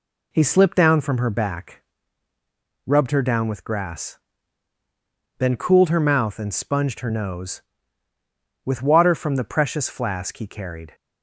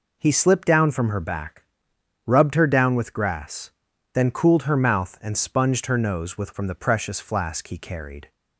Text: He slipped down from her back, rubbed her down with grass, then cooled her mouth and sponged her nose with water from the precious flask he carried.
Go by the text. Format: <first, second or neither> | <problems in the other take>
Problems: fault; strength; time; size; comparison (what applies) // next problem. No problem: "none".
first | skips "water"; at 6.5 s